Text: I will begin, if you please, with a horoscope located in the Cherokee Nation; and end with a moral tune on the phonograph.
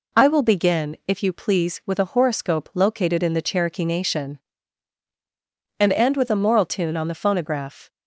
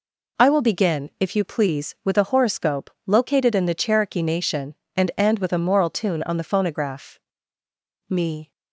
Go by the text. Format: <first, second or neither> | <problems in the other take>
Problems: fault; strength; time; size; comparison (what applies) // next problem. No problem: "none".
first | pauses between "horoscope" and "located"; slight; at 2.8 s; 0.18 s long // goes on to say "Me"; slight; from 8.0 s on; 0.42 s long